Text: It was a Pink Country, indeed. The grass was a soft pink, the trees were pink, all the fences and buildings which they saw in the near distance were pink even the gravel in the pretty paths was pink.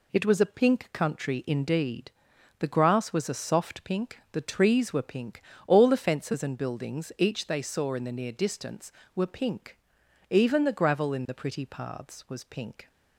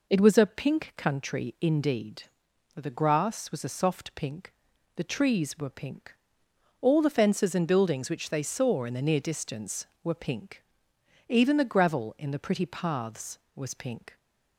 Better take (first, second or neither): second